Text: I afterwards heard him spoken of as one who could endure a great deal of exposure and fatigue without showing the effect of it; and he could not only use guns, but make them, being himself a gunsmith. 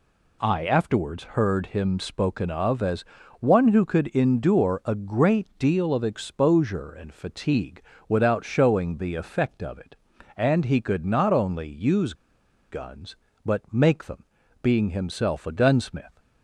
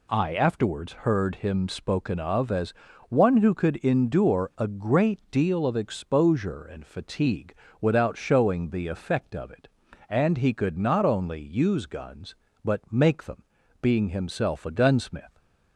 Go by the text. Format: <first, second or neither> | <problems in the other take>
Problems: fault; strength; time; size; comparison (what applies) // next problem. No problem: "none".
second | pauses between "as" and "one"; slight; at 3.0 s; 0.36 s long; slight in the second // pauses between "fatigue" and "without"; slight; at 7.8 s; 0.26 s long; slight in the second // pauses between "use" and "guns"; noticeable; at 12.1 s; 0.56 s long